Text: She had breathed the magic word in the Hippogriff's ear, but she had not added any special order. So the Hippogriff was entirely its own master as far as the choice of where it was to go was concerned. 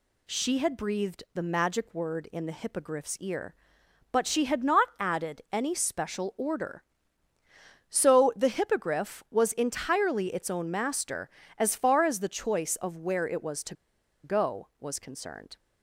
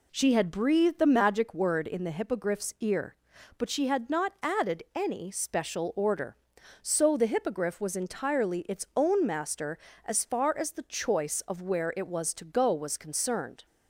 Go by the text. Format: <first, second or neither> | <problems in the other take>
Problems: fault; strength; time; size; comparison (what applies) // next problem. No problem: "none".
second | pauses between "to" and "go"; noticeable; at 13.7 s; 0.49 s long